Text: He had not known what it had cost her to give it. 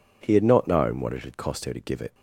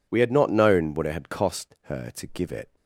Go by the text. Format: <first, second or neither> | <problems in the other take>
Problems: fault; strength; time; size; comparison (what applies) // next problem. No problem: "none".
first | says "We" for "He"; at 0.0 s